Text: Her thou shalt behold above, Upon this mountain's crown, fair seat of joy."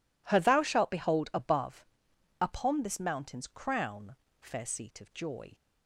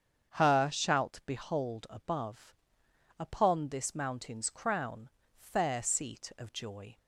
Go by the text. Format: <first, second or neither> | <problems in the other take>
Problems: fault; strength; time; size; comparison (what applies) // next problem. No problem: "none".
first | starts louder than the rest; strong; until 1.3 s; 7.5 dB // skips "thou"; at 0.6 s